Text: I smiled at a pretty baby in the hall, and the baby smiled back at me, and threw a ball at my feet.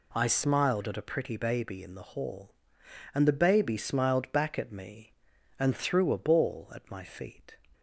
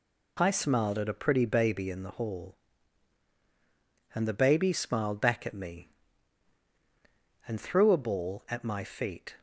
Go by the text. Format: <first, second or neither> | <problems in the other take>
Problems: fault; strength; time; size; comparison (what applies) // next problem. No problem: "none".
neither | none